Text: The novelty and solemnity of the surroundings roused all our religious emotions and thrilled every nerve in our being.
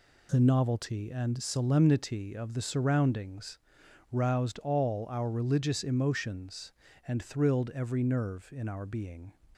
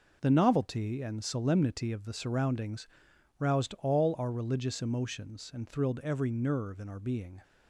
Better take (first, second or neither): neither